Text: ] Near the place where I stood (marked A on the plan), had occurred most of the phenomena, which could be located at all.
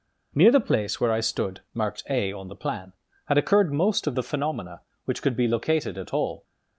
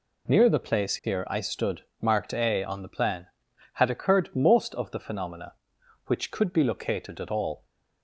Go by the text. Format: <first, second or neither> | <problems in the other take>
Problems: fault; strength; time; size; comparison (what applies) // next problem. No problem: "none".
first | says "here" for "where"; at 1.0 s